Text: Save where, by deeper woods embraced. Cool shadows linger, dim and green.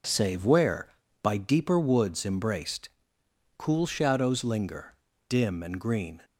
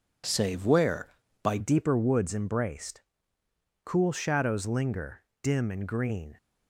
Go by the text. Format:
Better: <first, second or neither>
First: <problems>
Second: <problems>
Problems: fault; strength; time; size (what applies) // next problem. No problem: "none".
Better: first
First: none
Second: changes voice at "deeper"; from 1.5 s on; 4.8 s long